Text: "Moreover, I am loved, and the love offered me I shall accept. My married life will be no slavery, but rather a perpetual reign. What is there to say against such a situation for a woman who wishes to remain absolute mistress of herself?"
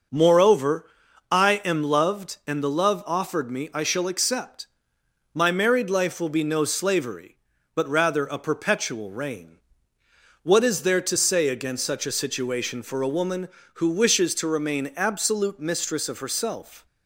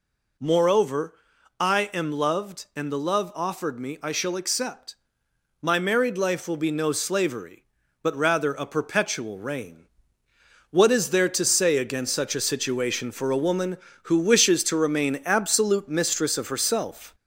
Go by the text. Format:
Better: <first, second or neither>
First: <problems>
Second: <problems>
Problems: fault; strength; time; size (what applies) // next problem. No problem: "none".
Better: first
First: none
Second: gets louder; slight; throughout; 3 dB